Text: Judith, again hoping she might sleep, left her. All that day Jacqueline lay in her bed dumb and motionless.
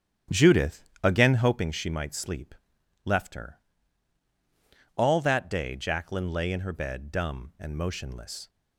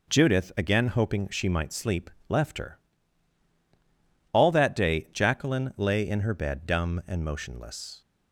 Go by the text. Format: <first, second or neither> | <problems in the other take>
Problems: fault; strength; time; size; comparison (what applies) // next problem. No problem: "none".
second | starts louder than the rest; strong; until 1.7 s; 11 dB